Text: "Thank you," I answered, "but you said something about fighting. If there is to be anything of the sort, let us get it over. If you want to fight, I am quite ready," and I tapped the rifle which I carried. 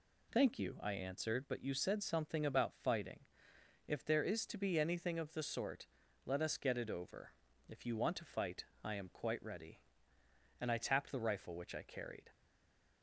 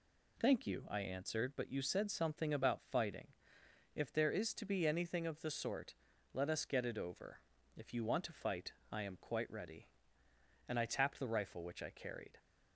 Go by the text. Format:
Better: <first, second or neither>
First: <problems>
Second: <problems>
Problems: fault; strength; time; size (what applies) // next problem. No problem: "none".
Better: second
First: stays silent after the last word; slight; from 12.3 s on; 0.7 s long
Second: none